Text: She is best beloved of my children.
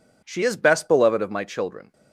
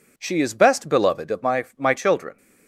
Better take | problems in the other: first | says "my" twice; at 1.7 s

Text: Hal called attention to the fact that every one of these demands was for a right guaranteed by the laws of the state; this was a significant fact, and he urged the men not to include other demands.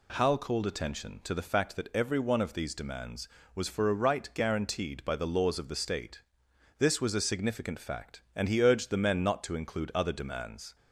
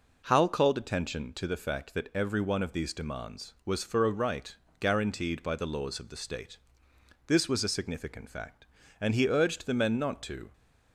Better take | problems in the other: first | pauses between "right" and "guaranteed"; slight; at 4.5 s; 0.24 s long // stops before "include other demands"; at 10.5 s

